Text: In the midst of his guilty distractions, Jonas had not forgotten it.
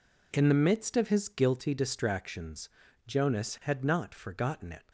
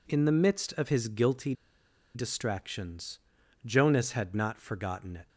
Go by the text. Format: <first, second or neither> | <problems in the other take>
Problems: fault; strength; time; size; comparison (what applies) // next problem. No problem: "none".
first | pauses between "guilty" and "distractions"; noticeable; at 1.5 s; 0.62 s long